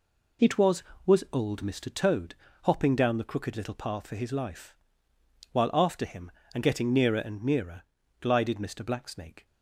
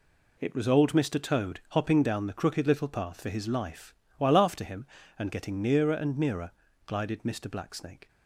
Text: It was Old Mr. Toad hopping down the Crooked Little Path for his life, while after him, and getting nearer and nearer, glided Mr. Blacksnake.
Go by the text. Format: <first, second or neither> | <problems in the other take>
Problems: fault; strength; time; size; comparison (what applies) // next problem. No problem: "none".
second | says "was" twice; at 1.0 s // pauses between "Toad" and "hopping"; slight; at 2.3 s; 0.28 s long